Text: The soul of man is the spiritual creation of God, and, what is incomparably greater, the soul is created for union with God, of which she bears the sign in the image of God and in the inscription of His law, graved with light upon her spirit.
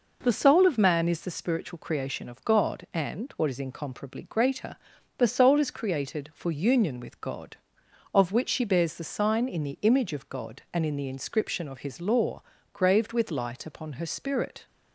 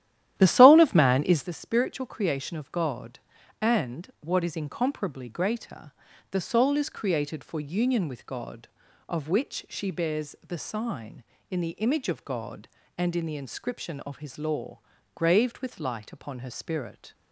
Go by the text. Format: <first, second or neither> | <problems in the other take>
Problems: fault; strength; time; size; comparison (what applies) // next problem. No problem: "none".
first | starts louder than the rest; strong; until 1.5 s; 12.5 dB